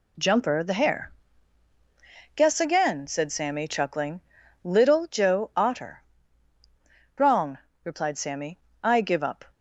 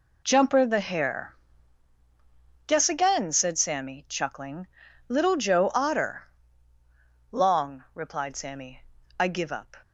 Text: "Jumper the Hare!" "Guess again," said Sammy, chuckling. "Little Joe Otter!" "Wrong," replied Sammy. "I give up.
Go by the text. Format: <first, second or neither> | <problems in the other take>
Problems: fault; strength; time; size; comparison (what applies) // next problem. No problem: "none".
first | says "Long" for "Wrong"; at 7.3 s